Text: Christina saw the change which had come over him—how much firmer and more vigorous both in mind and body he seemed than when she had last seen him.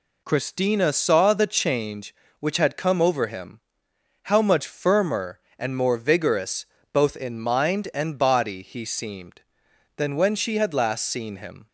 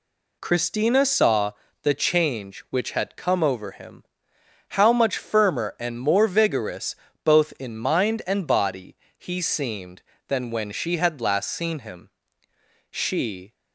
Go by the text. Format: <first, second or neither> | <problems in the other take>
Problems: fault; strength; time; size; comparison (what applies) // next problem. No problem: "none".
first | pauses between "saw" and "the"; slight; at 1.5 s; 0.30 s long // pauses between "vigorous" and "both"; slight; at 6.9 s; 0.28 s long; slight in the first // pauses between "body" and "he"; slight; at 8.9 s; 0.22 s long // goes on to say "She"; noticeable; from 12.8 s on; 0.64 s long